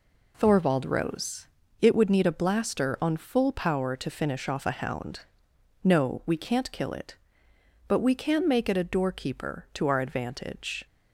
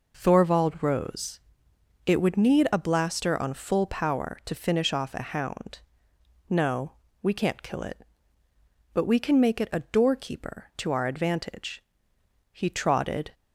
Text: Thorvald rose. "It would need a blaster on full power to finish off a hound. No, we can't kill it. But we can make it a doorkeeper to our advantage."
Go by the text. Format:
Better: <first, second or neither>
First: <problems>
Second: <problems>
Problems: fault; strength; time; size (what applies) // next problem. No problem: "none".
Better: first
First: none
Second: goes on to say "He trotted"; noticeable; from 12.5 s on; 0.80 s long